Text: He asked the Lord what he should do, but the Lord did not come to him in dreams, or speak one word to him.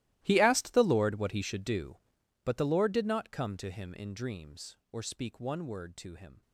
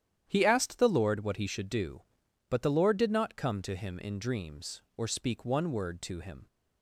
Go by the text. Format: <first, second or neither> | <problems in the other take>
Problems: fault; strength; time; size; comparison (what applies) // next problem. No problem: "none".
second | gets quieter; strong; throughout; 19.5 dB // starts louder than the rest; strong; until 1.2 s; 16.5 dB; strong in the second